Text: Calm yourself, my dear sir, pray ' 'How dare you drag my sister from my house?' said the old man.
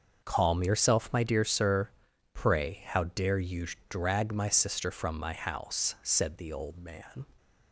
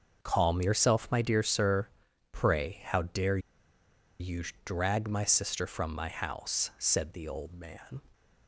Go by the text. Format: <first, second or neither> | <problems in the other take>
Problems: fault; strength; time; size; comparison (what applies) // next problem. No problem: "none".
first | starts louder than the rest; noticeable; until 1.2 s; 6 dB; noticeable in the first // pauses between "dare" and "you"; noticeable; at 3.3 s; 0.81 s long // pauses between "you" and "drag"; slight; at 4.4 s; 0.22 s long; slight in the first